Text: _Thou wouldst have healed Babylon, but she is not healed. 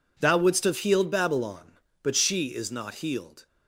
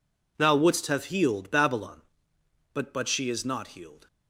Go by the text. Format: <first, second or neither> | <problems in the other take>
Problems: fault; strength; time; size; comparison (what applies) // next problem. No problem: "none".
first | says "but" twice; at 2.9 s